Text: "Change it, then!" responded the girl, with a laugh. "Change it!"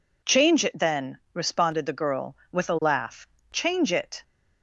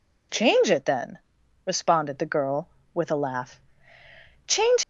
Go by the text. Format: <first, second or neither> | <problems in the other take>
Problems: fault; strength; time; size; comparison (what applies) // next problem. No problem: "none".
first | stops before "it"; at 4.8 s